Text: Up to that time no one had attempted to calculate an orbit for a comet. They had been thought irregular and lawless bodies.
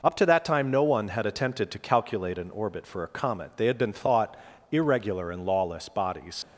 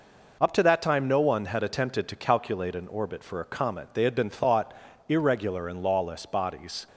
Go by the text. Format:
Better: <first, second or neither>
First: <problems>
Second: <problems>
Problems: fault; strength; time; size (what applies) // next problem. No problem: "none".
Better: second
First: pauses between "thought" and "irregular"; slight; at 4.3 s; 0.34 s long // leaves "bodies" unfinished; at 6.4 s; 70 ms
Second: pauses between "thought" and "irregular"; slight; at 4.7 s; 0.34 s long